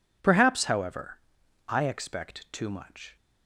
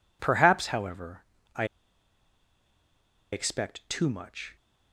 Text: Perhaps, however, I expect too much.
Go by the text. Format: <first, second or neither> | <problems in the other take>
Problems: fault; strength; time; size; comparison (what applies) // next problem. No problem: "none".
first | pauses between "I" and "expect"; strong; at 1.6 s; 1.6 s long